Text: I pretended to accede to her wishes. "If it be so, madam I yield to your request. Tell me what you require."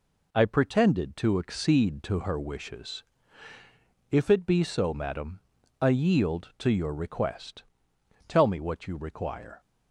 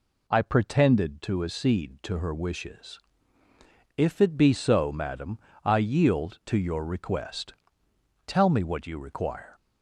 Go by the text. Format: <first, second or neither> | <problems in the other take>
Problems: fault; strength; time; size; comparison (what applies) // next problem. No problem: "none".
second | gets quieter; throughout; 4 dB // pauses between "madam" and "I"; at 5.4 s; 0.40 s long; slight in the second